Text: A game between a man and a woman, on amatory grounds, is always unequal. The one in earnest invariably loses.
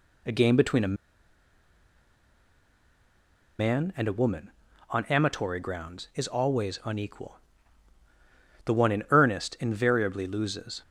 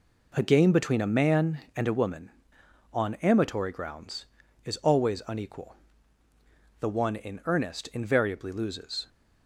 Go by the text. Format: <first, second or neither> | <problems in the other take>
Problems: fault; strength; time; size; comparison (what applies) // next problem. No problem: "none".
second | pauses between "a" and "man"; strong; at 0.9 s; 2.6 s long